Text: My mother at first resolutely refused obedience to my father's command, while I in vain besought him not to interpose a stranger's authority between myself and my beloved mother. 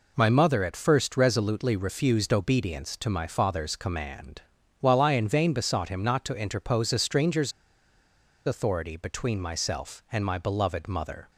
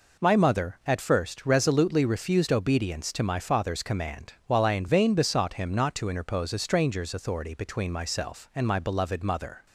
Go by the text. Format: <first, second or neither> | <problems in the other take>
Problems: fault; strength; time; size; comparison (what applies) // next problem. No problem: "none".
second | pauses between "stranger's" and "authority"; noticeable; at 7.5 s; 0.94 s long